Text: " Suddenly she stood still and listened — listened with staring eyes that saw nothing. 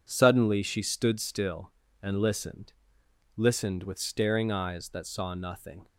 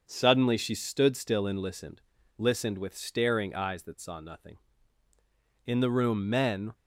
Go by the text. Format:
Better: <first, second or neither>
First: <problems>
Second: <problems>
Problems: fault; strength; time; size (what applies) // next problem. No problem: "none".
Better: first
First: none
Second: starts louder than the rest; until 1.0 s; 6.5 dB // goes on to say "In the room men"; noticeable; from 5.6 s on; 1.0 s long